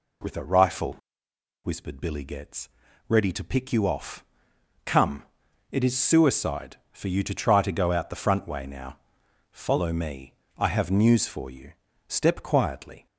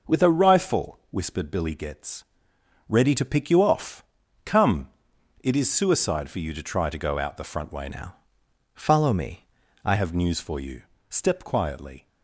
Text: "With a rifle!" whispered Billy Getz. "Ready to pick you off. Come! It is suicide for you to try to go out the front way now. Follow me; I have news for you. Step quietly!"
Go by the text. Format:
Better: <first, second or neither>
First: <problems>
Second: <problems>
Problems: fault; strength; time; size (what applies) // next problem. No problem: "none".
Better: first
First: none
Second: changes voice from "now" to "I"; from 7.9 to 9.9 s; 2.0 s long